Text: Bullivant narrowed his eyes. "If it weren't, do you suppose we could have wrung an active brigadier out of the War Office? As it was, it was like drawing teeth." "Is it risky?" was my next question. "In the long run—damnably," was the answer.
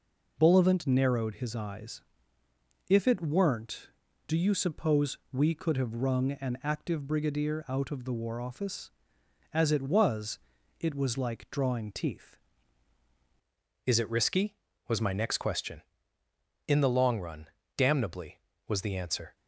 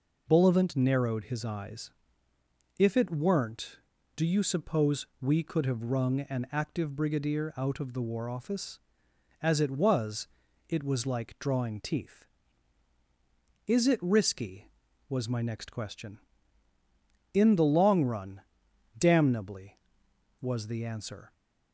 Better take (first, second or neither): second